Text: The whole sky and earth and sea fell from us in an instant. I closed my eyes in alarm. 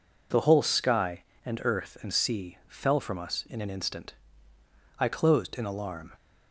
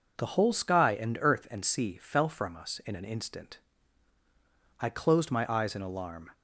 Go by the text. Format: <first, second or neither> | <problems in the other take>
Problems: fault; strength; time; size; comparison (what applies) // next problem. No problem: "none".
second | skips "my eyes"; at 5.5 s